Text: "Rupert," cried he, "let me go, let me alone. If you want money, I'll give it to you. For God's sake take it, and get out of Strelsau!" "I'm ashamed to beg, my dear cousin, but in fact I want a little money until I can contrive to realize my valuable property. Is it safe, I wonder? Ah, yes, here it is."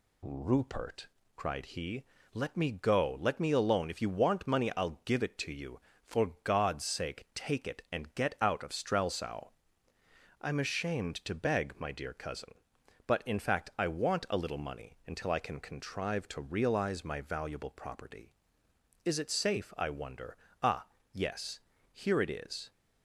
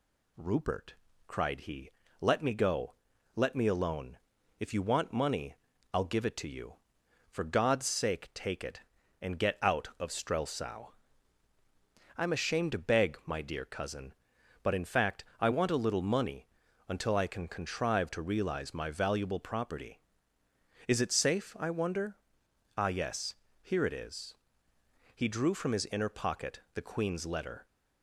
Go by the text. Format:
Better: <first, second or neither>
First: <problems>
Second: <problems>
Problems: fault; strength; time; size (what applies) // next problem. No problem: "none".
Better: first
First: none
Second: pauses between "money" and "until"; at 16.4 s; 0.40 s long // goes on to say "He drew from his inner pocket the queen's letter"; strong; from 25.1 s on; 2.5 s long